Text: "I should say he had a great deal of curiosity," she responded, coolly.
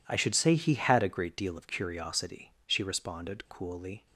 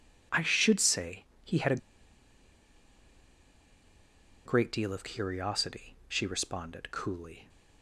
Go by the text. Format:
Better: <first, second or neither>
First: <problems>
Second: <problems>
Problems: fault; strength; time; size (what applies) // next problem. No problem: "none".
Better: first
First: none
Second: pauses between "say" and "he"; slight; at 1.2 s; 0.22 s long // pauses between "a" and "great"; strong; at 1.7 s; 2.6 s long